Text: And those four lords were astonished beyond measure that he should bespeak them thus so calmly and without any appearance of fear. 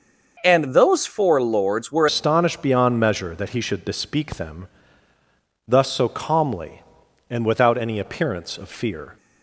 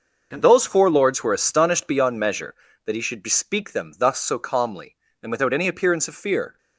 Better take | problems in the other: second | starts louder than the rest; until 1.4 s; 6 dB; noticeable in the second // changes voice at "astonished"; from 2.0 s on; 7.1 s long // pauses between "them" and "thus"; at 4.6 s; 1.0 s long

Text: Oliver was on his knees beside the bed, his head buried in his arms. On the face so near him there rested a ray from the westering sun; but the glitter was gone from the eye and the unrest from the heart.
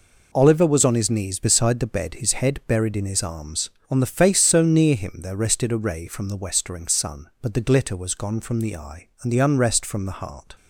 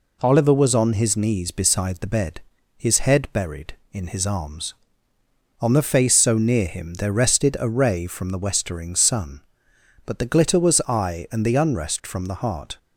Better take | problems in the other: first | skips "gone from the"; at 10.8 s

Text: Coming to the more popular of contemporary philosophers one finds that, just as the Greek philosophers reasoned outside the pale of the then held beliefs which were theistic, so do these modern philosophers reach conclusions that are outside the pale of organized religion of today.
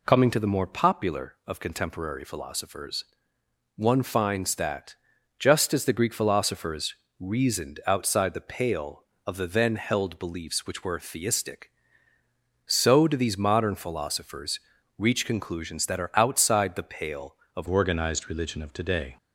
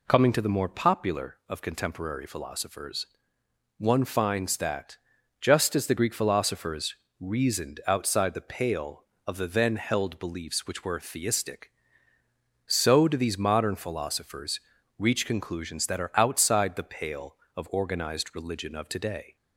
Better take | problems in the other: second | pauses between "philosophers" and "one"; noticeable; at 3.0 s; 0.70 s long; noticeable in the second // pauses between "philosophers" and "reasoned"; slight; at 6.9 s; 0.26 s long; slight in the second // pauses between "philosophers" and "reach"; at 14.5 s; 0.40 s long; also in the second // changes voice at "organized"; from 17.6 s on; 1.5 s long

